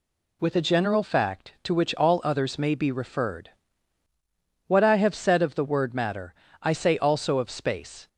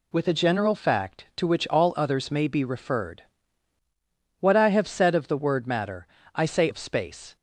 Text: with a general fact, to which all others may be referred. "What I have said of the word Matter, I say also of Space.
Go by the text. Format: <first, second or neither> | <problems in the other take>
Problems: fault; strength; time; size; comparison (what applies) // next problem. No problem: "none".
first | skips "also"; at 6.6 s